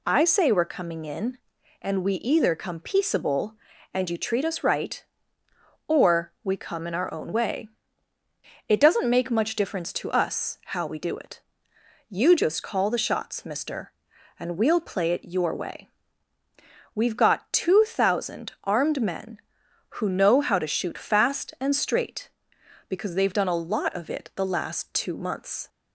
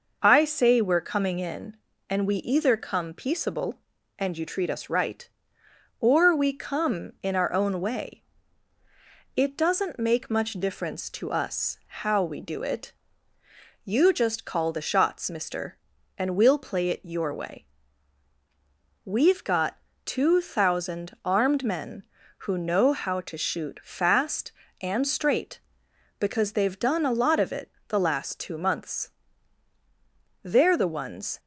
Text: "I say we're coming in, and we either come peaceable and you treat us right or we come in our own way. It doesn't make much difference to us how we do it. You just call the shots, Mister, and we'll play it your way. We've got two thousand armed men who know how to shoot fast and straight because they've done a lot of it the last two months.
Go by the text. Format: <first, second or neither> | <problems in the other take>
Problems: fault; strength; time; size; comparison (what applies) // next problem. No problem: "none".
first | pauses between "got" and "two"; slight; at 19.7 s; 0.26 s long // pauses between "it" and "the"; slight; at 27.7 s; 0.18 s long // goes on to say "They're the ones"; noticeable; from 30.4 s on; 0.96 s long